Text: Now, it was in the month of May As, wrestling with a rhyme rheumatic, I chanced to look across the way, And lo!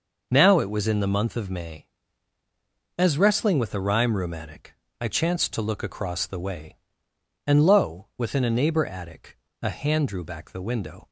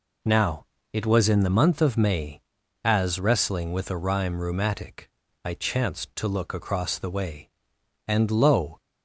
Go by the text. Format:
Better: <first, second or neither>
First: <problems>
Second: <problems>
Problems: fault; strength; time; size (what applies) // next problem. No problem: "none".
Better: second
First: goes on to say "within a neighbor attic A hand drew back the window"; strong; from 8.1 s on; 2.9 s long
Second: none